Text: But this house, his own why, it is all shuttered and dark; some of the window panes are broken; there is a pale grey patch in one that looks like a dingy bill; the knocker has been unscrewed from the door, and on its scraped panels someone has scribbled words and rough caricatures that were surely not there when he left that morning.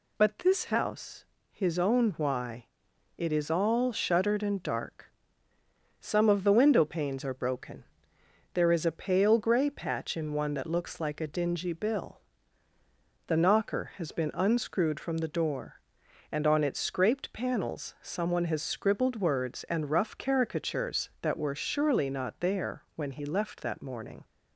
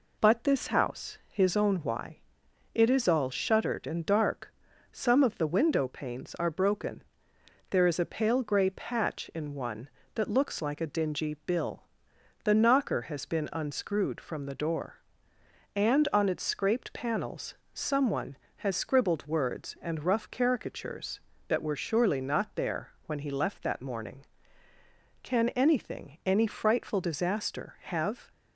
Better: first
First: none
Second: pauses between "panels" and "someone"; slight; at 17.5 s; 0.22 s long // pauses between "there" and "when"; slight; at 22.8 s; 0.16 s long // goes on to say "Can anything any frightful disaster have"; strong; from 25.2 s on; 3.1 s long

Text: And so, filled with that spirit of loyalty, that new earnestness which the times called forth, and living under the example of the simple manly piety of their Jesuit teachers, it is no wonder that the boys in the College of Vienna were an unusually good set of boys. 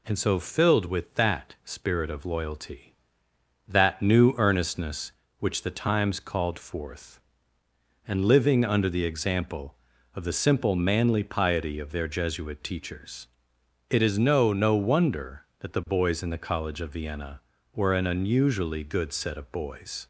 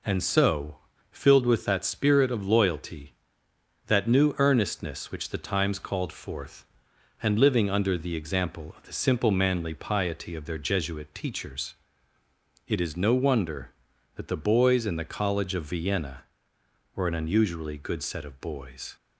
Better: second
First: says "no" twice; at 14.5 s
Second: none

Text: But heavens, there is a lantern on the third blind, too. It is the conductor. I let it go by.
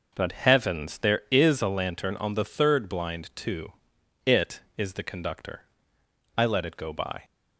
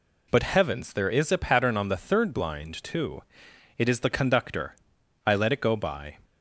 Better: first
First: none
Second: says "pattern" for "lantern"; at 1.3 s

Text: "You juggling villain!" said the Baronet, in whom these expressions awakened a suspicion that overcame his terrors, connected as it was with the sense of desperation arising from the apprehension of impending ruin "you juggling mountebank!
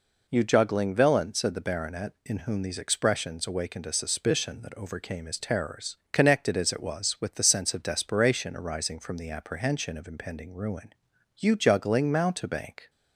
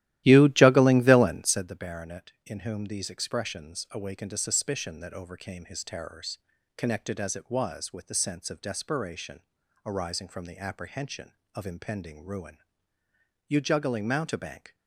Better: first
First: pauses between "ruin" and "you"; at 10.9 s; 0.44 s long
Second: starts louder than the rest; strong; until 1.8 s; 14.5 dB // pauses between "desperation" and "arising"; at 9.4 s; 0.44 s long // pauses between "ruin" and "you"; noticeable; at 12.5 s; 0.90 s long

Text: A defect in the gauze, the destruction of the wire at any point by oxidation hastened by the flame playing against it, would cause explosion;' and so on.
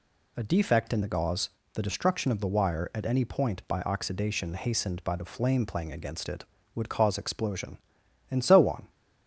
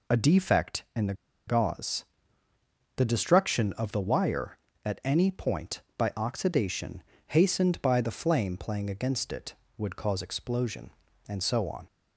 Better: first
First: none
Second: pauses between "the" and "gauze"; slight; at 1.1 s; 0.34 s long // pauses between "oxidation" and "hastened"; slight; at 7.0 s; 0.26 s long

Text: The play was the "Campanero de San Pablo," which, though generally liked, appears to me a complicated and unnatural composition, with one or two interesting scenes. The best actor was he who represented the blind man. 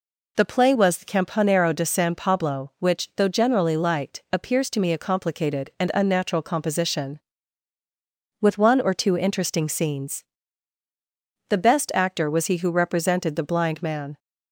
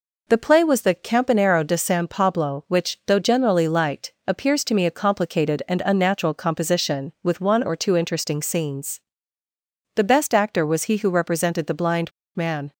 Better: first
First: none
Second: pauses between "blind" and "man"; slight; at 12.1 s; 0.24 s long

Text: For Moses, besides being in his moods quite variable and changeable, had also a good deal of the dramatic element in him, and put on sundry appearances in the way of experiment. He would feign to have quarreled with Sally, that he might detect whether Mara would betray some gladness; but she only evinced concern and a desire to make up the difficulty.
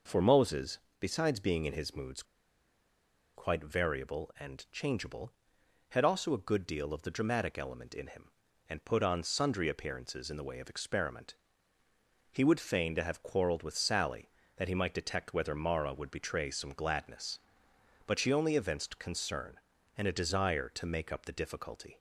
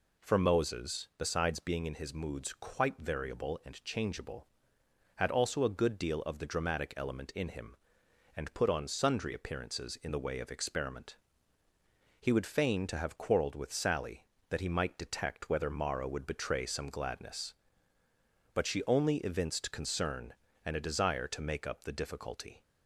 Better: second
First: pauses between "moods" and "quite"; at 2.2 s; 1.1 s long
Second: none

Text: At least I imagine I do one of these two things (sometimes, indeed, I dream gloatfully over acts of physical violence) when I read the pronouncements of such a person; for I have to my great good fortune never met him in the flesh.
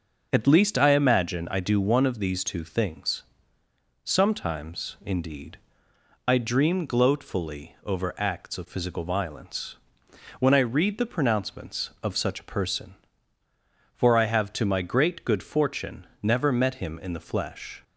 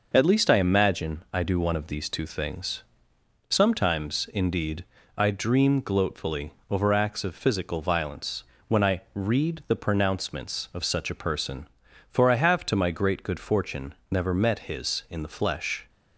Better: first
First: pauses between "fortune" and "never"; slight; at 16.0 s; 0.16 s long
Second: pauses between "gloatfully" and "over"; slight; at 6.5 s; 0.16 s long // pauses between "fortune" and "never"; slight; at 13.9 s; 0.16 s long // says "his" for "him"; at 14.6 s

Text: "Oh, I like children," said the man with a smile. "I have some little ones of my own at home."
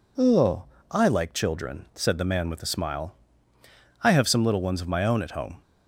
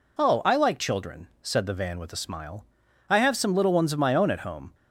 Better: first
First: none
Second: says "van" for "man"; at 1.7 s

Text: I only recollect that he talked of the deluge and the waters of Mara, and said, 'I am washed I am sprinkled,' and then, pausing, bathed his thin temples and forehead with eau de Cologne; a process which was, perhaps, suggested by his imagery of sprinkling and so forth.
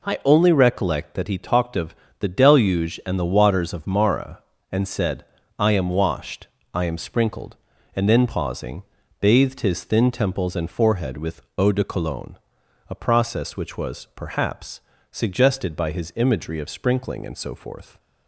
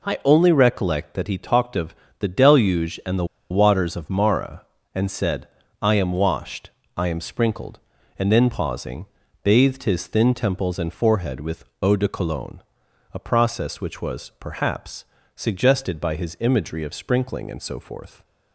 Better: first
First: pauses between "of" and "the"; slight; at 1.9 s; 0.24 s long // pauses between "washed" and "I"; slight; at 6.4 s; 0.26 s long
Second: pauses between "of" and "the"; slight; at 1.9 s; 0.24 s long // pauses between "the" and "waters"; slight; at 3.2 s; 0.25 s long // pauses between "washed" and "I"; slight; at 6.6 s; 0.26 s long // pauses between "with" and "eau"; slight; at 11.6 s; 0.16 s long

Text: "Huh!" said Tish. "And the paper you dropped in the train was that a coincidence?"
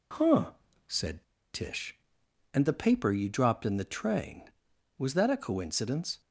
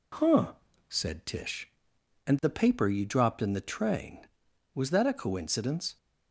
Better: second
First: pauses between "said" and "Tish"; slight; at 1.2 s; 0.29 s long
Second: none

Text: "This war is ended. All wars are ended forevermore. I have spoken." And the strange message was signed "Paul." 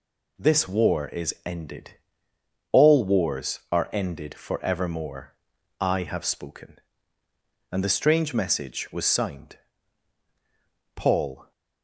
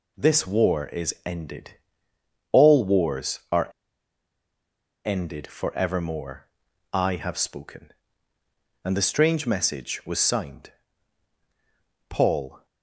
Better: first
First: pauses between "signed" and "Paul"; strong; at 9.5 s; 1.3 s long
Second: pauses between "are" and "ended"; strong; at 3.7 s; 1.3 s long // pauses between "signed" and "Paul"; strong; at 10.7 s; 1.3 s long

